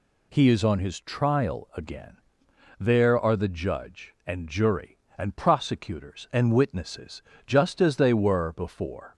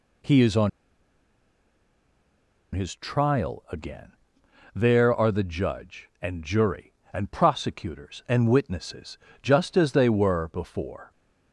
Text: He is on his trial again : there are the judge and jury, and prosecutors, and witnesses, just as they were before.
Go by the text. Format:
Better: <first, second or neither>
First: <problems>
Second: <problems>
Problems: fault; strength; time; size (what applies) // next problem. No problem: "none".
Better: first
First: none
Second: pauses between "on" and "his"; strong; at 0.6 s; 2.0 s long